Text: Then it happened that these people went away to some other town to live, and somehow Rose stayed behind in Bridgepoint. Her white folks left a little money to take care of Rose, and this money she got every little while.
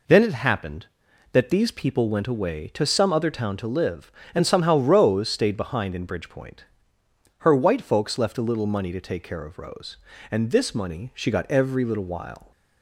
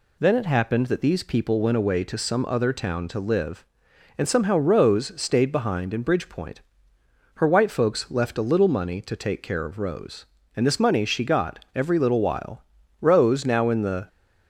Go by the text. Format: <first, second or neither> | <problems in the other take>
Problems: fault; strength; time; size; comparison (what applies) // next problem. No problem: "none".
first | goes on to say "Rose now in the"; noticeable; from 13.0 s on; 1.0 s long